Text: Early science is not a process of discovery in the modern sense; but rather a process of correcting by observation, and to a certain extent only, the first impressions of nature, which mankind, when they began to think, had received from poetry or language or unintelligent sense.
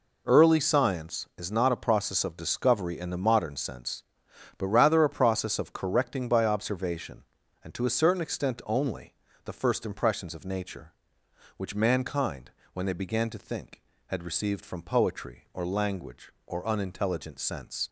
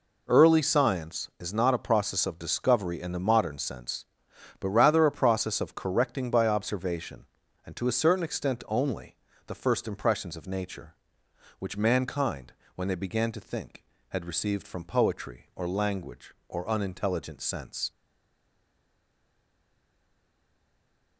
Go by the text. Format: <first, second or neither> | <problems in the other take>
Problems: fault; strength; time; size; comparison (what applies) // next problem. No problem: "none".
first | stays silent after the last word; strong; from 17.9 s on; 3.2 s long